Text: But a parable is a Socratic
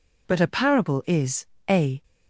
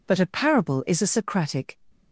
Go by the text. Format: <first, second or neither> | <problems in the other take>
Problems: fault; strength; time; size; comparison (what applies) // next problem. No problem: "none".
second | pauses between "is" and "a"; slight; at 1.4 s; 0.22 s long // stops before "Socratic"; at 2.0 s